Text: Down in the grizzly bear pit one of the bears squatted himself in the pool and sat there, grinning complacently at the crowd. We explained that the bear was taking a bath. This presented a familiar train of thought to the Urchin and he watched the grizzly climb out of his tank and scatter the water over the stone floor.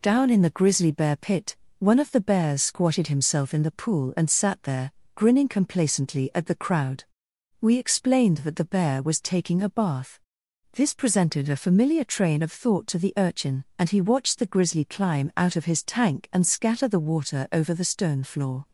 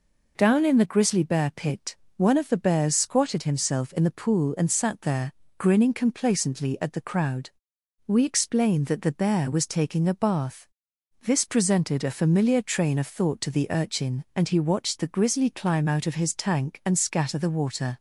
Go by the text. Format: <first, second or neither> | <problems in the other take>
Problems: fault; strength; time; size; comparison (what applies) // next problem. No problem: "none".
first | pauses between "pit" and "one"; slight; at 1.9 s; 0.22 s long; slight in the first // stops before "over the stone floor"; at 17.9 s